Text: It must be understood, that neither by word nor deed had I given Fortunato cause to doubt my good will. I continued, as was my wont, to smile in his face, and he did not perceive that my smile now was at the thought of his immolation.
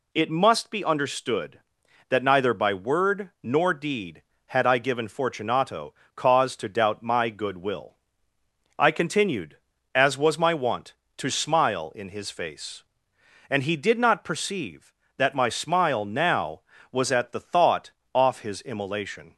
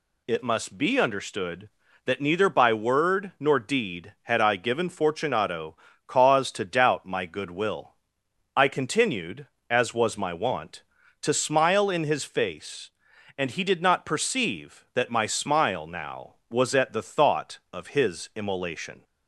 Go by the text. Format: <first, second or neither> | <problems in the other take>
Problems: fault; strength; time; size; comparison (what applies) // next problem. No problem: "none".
second | pauses between "Fortunato" and "cause"; slight; at 5.9 s; 0.22 s long; slight in the second // says "off" for "of"; at 18.1 s